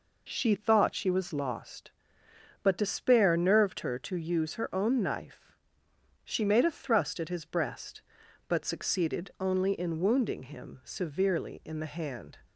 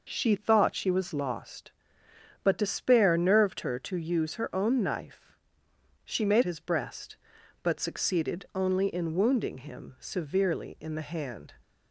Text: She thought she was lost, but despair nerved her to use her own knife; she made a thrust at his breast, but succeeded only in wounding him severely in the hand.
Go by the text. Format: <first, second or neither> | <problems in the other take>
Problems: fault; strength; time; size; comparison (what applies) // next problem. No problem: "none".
first | skips "a thrust at"; at 6.4 s